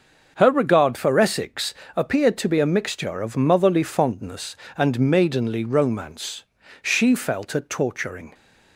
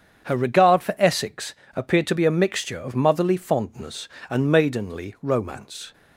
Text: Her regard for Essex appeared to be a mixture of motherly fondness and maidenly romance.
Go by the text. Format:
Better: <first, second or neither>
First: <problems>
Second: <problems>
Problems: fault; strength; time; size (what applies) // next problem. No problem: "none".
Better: second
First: starts louder than the rest; until 1.3 s; 6.5 dB // pauses between "Essex" and "appeared"; slight; at 1.7 s; 0.20 s long // goes on to say "She felt a torturing"; from 6.8 s on; 1.5 s long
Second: starts louder than the rest; strong; until 1.3 s; 7.5 dB // pauses between "Essex" and "appeared"; slight; at 1.5 s; 0.22 s long